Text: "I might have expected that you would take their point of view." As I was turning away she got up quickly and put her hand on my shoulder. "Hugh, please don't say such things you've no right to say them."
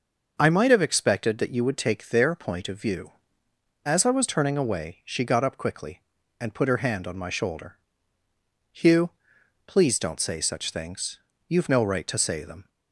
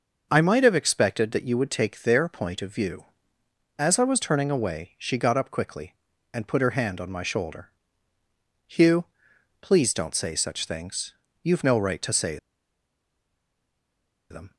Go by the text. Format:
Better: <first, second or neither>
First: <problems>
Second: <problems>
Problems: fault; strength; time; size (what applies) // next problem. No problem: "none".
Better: first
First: starts louder than the rest; noticeable; until 1.4 s; 6 dB // pauses between "things" and "you've"; slight; at 11.1 s; 0.26 s long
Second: starts louder than the rest; noticeable; until 1.3 s; 6 dB // pauses between "things" and "you've"; slight; at 11.1 s; 0.26 s long // pauses between "say" and "them"; strong; at 12.3 s; 1.9 s long